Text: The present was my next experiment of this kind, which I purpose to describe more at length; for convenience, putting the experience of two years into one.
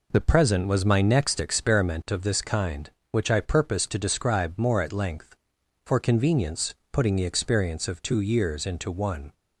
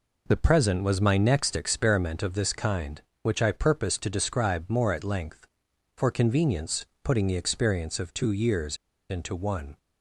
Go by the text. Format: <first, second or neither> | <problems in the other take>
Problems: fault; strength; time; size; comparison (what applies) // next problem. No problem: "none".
first | pauses between "years" and "into"; slight; at 8.7 s; 0.33 s long